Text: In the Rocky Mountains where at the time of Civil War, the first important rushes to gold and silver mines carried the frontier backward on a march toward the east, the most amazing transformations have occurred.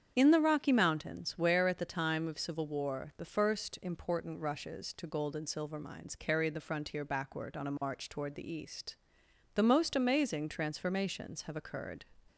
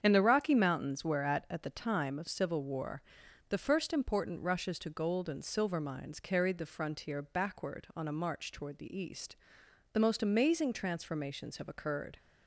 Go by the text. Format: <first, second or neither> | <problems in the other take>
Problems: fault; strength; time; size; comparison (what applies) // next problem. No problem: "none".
first | starts louder than the rest; strong; until 1.0 s; 8 dB; strong in the first // says "at" twice; at 1.5 s